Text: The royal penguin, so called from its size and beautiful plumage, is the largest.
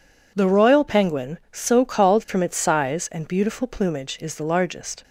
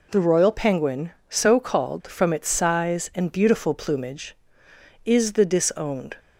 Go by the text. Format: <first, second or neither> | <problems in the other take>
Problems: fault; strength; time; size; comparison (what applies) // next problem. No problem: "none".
first | says "disowned" for "largest"; at 5.4 s